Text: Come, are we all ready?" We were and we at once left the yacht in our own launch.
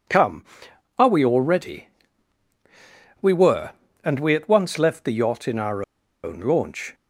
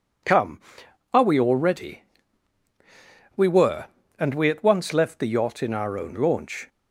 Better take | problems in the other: second | pauses between "our" and "own"; at 5.8 s; 0.40 s long

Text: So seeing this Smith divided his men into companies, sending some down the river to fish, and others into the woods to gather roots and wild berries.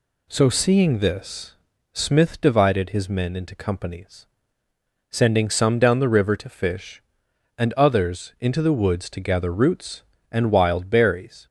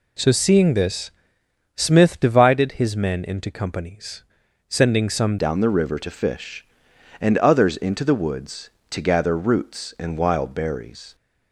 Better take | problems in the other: first | pauses between "this" and "Smith"; noticeable; at 1.1 s; 0.64 s long; also in the first // changes voice at "down"; from 5.3 s on; 5.8 s long

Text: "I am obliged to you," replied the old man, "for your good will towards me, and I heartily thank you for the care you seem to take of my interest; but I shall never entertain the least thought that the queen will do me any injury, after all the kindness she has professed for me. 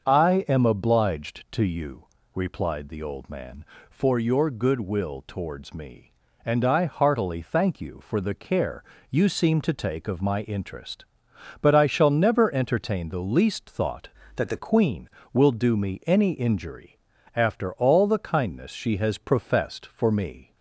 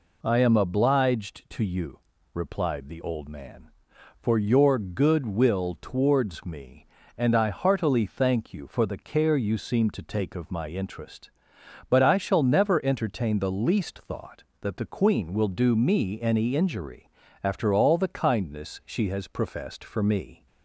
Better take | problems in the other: second | starts louder than the rest; until 1.1 s; 6.5 dB // pauses between "care" and "you"; slight; at 8.8 s; 0.30 s long // changes voice from "that" to "the"; from 14.3 to 14.5 s; 0.2 s long

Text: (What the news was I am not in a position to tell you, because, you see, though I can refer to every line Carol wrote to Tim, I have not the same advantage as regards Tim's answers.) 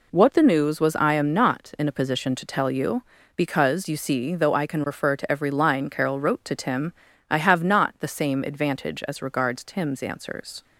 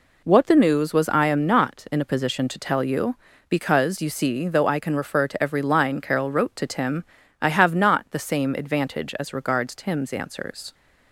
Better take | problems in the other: neither | none

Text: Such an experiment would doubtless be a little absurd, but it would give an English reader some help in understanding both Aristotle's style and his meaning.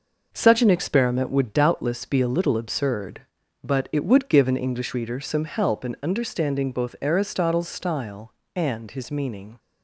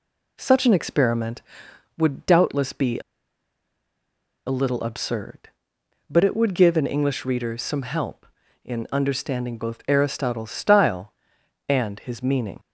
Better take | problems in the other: first | pauses between "a" and "little"; strong; at 3.0 s; 1.4 s long

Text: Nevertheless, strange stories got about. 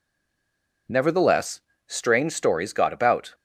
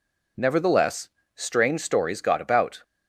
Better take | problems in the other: second | stays silent before the first word; slight; until 0.8 s; 0.8 s long

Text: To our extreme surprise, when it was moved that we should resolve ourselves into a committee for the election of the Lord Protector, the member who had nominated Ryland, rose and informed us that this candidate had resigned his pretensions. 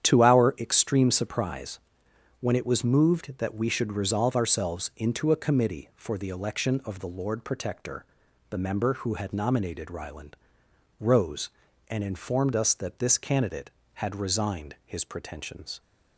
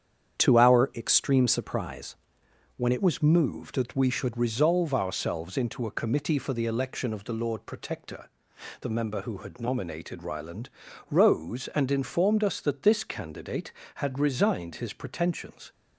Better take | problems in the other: first | starts louder than the rest; strong; until 1.4 s; 8.5 dB; strong in the first // changes voice at "was"; from 3.0 s on; 12.7 s long

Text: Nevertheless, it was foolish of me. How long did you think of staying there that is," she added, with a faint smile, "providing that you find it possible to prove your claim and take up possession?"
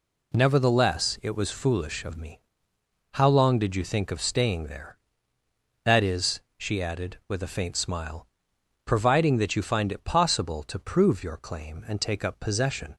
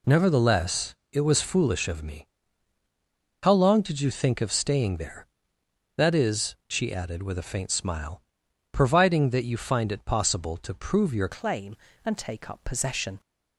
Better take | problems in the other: first | changes voice at "claim"; from 11.3 s on; 1.8 s long

